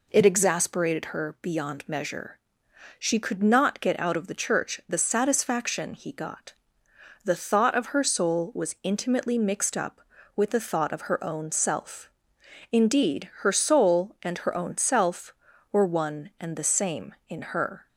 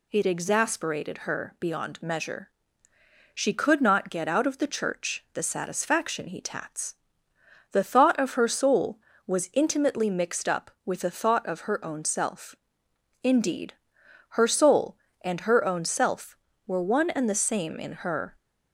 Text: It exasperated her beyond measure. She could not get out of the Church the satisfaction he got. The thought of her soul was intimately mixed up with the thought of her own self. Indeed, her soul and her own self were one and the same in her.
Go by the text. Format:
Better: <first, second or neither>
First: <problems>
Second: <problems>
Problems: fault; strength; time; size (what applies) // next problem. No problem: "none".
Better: first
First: none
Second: says "tats" for "got"; at 6.4 s